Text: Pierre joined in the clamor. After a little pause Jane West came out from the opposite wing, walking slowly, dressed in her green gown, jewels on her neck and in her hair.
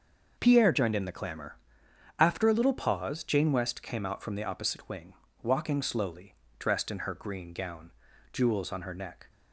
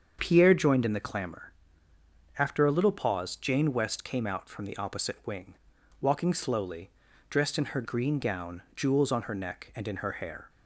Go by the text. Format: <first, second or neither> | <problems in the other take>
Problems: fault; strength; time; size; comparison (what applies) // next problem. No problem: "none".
second | starts louder than the rest; noticeable; until 1.3 s; 6 dB; also in the second // stops before "and in her hair"; at 9.2 s